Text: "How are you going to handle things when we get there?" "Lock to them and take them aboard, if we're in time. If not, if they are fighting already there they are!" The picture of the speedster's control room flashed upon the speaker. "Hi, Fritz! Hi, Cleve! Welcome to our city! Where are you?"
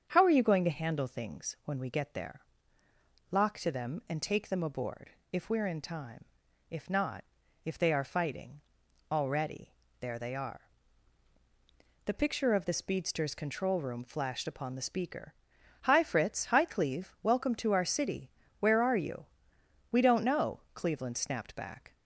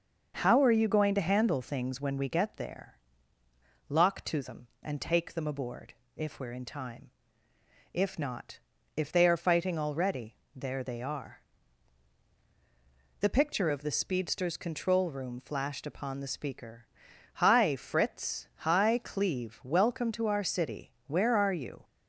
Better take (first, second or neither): second